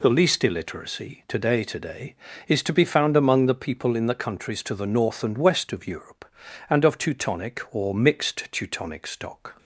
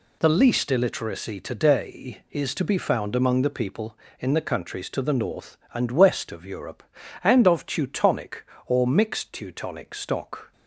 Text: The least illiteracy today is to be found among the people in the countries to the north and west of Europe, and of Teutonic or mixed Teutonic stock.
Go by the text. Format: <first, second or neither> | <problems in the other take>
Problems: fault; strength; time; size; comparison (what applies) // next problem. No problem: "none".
second | says "today" twice; at 1.6 s